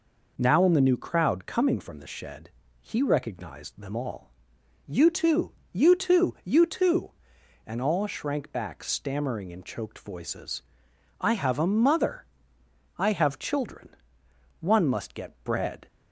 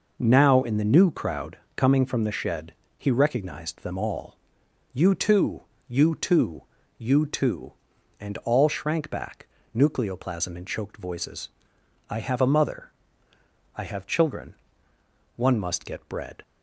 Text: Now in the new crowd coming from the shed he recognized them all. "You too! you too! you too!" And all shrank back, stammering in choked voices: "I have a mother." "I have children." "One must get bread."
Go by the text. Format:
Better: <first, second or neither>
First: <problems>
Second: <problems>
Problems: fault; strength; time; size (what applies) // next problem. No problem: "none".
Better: first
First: pauses between "shed" and "he"; slight; at 2.4 s; 0.32 s long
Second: pauses between "crowd" and "coming"; slight; at 1.5 s; 0.18 s long // pauses between "shed" and "he"; slight; at 2.7 s; 0.26 s long // says "nucleoplasm" for "stammering"; at 9.7 s